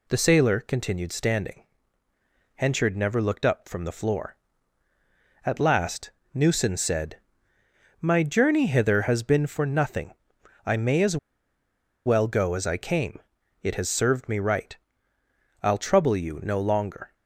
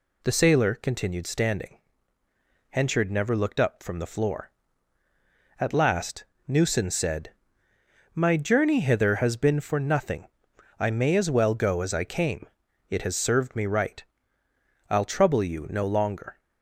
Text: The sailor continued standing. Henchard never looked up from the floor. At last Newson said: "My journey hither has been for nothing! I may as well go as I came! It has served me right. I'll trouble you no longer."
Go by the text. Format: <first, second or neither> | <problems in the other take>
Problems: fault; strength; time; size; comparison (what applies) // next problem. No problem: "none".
second | pauses between "last" and "Newson"; slight; at 6.1 s; 0.24 s long; slight in the second // pauses between "as" and "well"; noticeable; at 11.1 s; 0.89 s long